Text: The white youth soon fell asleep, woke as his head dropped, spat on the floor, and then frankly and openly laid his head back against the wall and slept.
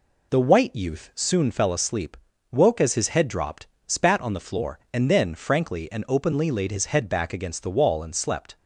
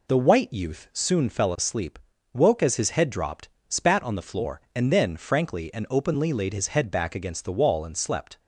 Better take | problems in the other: neither | none

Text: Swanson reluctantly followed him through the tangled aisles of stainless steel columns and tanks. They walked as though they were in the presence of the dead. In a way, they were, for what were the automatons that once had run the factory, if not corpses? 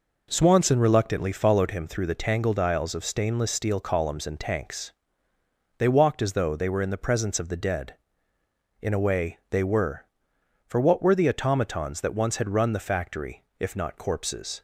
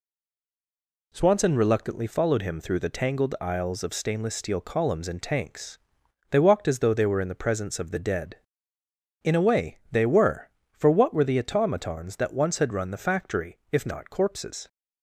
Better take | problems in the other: first | stays silent before the first word; until 1.1 s; 1.1 s long

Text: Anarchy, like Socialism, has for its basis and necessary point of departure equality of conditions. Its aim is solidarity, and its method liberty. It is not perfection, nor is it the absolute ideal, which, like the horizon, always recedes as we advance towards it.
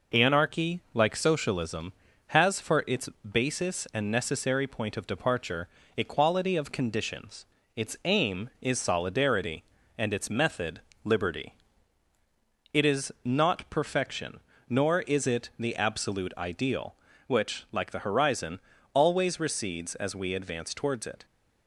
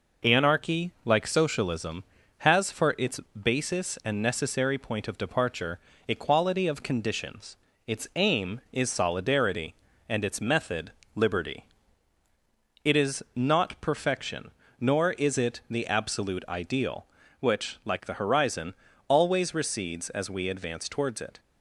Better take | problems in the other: neither | pauses between "its" and "basis"; slight; the same in both // pauses between "departure" and "equality"; slight; the same in both // pauses between "method" and "liberty"; slight; the same in both

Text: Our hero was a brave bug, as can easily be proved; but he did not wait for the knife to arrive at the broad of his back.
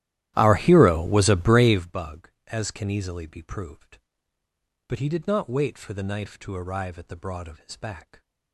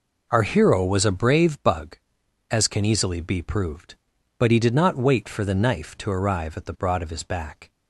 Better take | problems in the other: second | starts louder than the rest; strong; until 1.8 s; 13.5 dB

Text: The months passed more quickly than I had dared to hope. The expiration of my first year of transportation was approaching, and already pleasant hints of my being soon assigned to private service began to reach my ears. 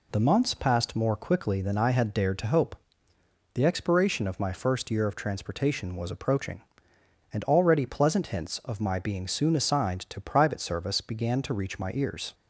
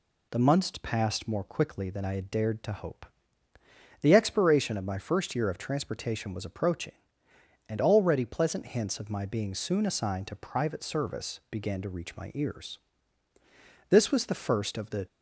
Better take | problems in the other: first | goes on to say "This was the first of the"; noticeable; from 13.8 s on; 1.1 s long

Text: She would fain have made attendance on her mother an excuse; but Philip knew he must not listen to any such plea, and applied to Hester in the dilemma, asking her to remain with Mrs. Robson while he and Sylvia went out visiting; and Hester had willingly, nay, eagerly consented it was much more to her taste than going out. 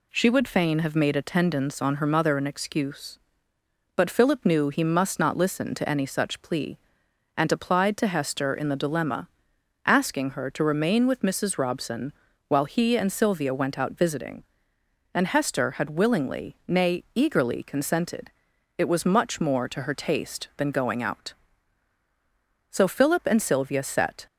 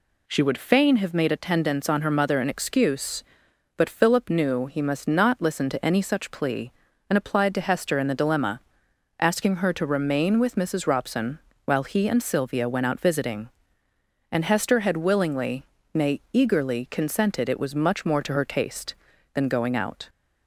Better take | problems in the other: second | pauses between "Robson" and "while"; slight; at 12.1 s; 0.36 s long; slight in the second // pauses between "consented" and "it"; noticeable; at 18.3 s; 0.46 s long // goes on to say "So Philip and Sylvia set"; from 22.7 s on; 1.5 s long

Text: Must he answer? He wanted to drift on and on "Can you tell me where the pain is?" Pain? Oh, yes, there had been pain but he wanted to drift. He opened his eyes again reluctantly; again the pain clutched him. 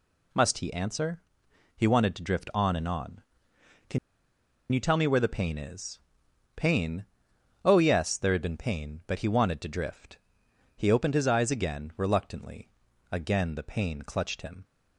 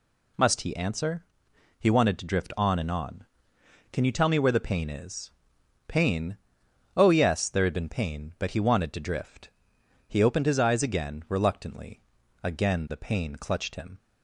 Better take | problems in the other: second | pauses between "Can" and "you"; noticeable; at 3.9 s; 0.73 s long

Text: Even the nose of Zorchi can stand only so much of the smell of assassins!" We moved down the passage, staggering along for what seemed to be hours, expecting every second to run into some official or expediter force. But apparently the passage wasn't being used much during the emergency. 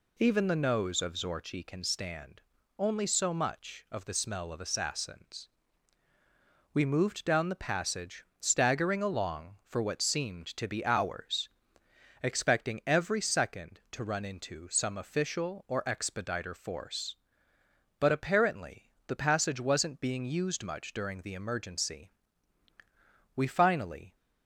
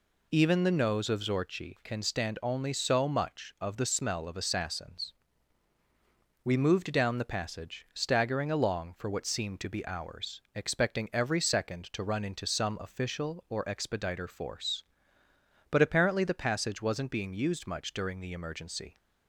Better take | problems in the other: second | pauses between "stand" and "only"; at 2.4 s; 0.38 s long // pauses between "apparently" and "the"; slight; at 18.8 s; 0.18 s long // goes on to say "We finally"; noticeable; from 23.3 s on; 0.80 s long

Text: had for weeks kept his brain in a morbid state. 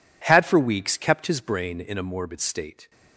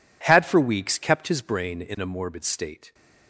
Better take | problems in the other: neither | none

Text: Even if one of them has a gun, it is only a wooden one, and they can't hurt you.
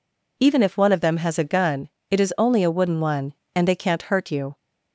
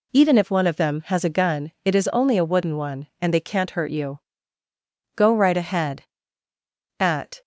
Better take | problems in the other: first | goes on to say "Go right ahead At"; strong; from 5.1 s on; 2.2 s long

